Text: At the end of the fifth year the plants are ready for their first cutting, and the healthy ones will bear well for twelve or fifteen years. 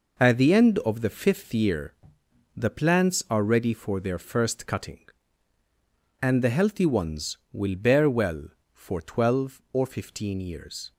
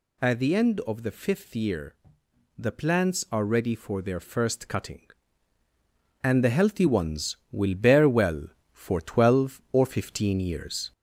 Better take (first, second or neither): first